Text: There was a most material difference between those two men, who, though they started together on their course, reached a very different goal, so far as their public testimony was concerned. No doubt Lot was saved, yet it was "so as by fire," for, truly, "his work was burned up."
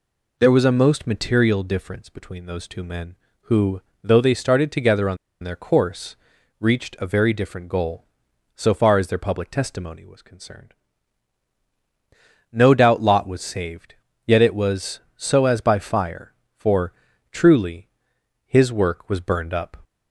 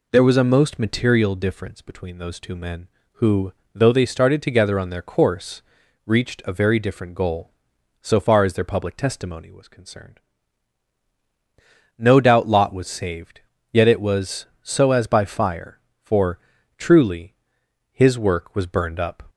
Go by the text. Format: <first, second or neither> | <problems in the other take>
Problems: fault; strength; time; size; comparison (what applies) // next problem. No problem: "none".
second | pauses between "on" and "their"; slight; at 5.1 s; 0.26 s long